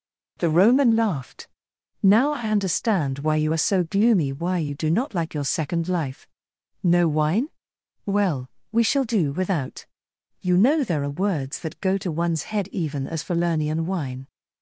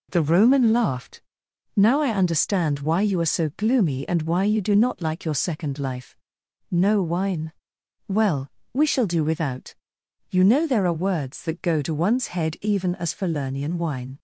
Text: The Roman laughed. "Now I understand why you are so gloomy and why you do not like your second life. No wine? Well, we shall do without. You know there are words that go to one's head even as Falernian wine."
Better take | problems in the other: second | skips "and"; at 4.3 s

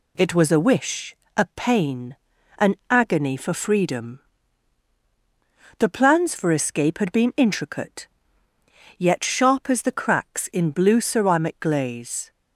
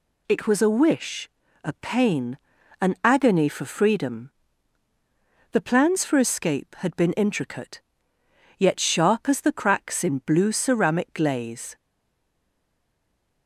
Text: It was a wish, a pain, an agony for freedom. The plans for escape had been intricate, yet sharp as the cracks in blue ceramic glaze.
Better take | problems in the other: first | stays silent after the last word; noticeable; from 11.7 s on; 1.7 s long

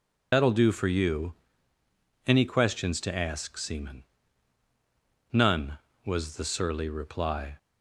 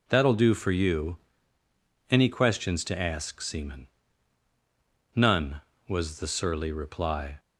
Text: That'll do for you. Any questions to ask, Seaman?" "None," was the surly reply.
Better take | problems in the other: second | loses the start of "That'll"; at 0.3 s; 65 ms

